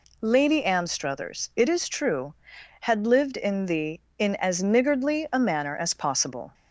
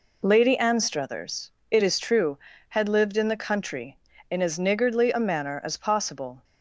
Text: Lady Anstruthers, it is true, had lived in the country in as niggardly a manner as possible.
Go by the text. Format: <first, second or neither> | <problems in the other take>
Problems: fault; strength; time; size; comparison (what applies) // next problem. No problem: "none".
second | skips "country"; at 4.0 s